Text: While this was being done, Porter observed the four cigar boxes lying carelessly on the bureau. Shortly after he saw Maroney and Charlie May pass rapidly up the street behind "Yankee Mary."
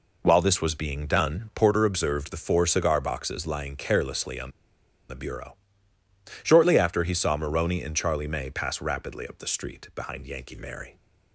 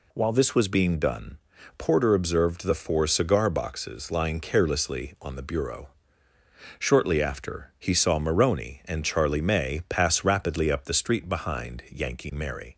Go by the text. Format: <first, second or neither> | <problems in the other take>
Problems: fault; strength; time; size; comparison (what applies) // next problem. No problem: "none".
second | pauses between "on" and "the"; noticeable; at 4.5 s; 0.58 s long